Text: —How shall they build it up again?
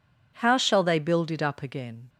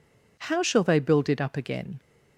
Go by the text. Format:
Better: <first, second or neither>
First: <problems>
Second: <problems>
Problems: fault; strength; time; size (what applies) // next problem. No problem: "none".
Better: neither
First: none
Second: none